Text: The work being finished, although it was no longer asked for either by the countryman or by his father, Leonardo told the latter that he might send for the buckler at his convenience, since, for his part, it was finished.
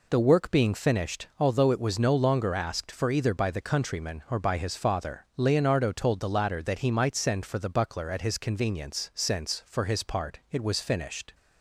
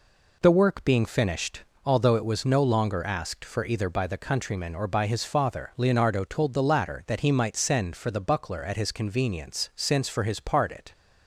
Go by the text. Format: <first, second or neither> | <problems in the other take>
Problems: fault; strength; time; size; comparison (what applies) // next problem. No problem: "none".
first | stops before "was finished"; at 10.9 s